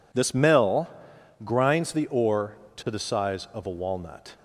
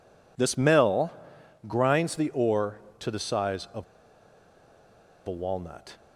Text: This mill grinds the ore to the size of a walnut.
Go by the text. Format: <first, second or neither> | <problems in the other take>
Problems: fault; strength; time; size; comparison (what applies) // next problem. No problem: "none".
first | pauses between "mill" and "grinds"; noticeable; at 1.1 s; 0.52 s long; noticeable in the first // pauses between "of" and "a"; strong; at 3.8 s; 1.4 s long